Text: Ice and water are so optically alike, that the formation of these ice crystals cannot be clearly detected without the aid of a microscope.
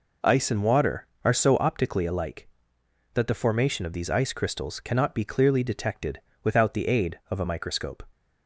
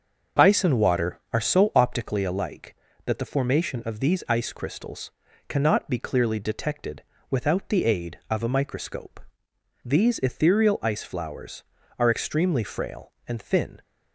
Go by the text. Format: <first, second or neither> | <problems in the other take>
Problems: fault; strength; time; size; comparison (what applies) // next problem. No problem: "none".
first | pauses between "crystals" and "cannot"; at 5.0 s; 0.38 s long // pauses between "detected" and "without"; slight; at 7.0 s; 0.30 s long; slight in the first // goes on to say "These ethereal ice flowers are extremely frail and thin"; strong; from 9.8 s on; 3.9 s long